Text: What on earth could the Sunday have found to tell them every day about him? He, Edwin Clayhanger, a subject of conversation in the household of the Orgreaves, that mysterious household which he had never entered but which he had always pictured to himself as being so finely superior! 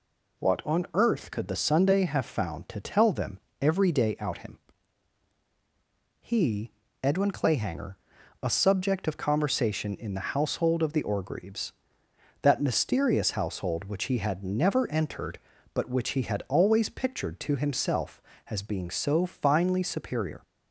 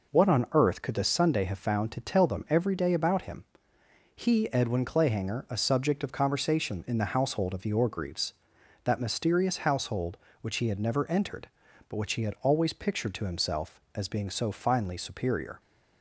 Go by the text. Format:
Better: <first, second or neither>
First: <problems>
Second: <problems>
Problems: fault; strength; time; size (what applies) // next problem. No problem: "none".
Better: second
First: pauses between "them" and "every"; slight; at 3.4 s; 0.20 s long // says "out" for "about"; at 4.2 s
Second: none